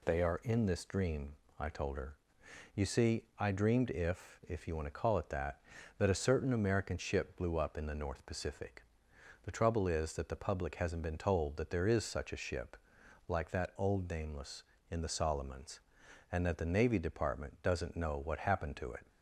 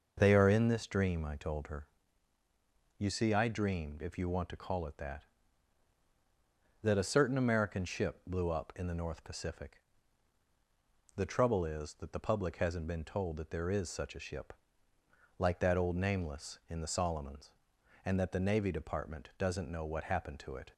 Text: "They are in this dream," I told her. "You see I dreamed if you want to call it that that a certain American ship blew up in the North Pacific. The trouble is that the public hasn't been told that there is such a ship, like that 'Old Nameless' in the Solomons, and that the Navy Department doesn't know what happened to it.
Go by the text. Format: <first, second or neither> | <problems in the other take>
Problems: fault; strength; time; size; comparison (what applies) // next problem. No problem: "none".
second | pauses between "see" and "I"; slight; at 3.2 s; 0.16 s long // says "if" twice; at 4.4 s